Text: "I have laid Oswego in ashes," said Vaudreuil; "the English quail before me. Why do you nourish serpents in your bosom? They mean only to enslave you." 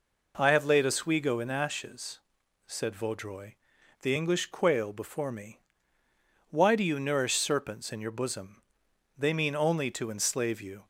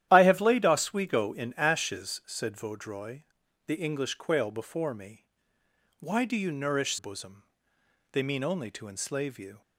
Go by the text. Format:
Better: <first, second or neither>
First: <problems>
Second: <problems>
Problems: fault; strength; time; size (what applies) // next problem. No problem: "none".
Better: first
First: none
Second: starts louder than the rest; strong; until 1.1 s; 11.5 dB // skips "serpents in your"; at 6.9 s